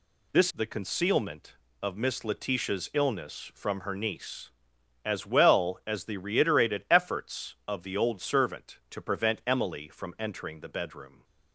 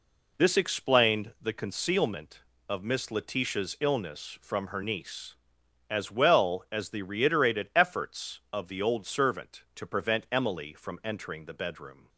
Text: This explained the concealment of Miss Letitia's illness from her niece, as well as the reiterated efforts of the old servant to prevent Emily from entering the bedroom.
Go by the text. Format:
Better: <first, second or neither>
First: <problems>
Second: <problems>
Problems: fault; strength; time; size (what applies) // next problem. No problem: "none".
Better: second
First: skips "explained"; at 0.5 s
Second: none